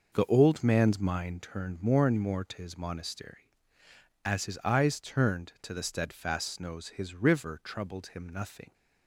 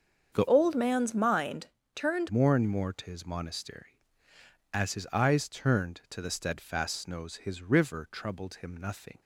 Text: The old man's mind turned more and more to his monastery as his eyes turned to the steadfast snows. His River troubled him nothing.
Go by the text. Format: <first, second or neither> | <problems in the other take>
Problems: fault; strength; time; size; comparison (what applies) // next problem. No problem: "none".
first | starts louder than the rest; until 1.3 s; 7 dB // changes voice from "old" to "turned"; from 0.4 to 2.2 s; 1.8 s long // pauses between "mind" and "turned"; slight; at 1.6 s; 0.26 s long